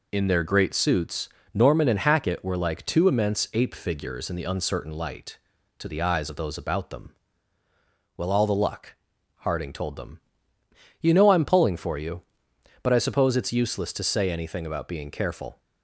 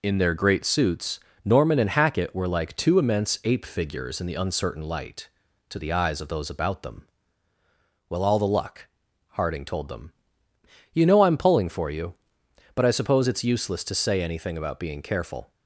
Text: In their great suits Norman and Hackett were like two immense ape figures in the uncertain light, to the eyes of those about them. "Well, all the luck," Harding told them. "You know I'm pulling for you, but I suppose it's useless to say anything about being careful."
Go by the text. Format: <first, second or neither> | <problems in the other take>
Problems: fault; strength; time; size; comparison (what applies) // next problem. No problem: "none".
neither | pauses between "suits" and "Norman"; slight; the same in both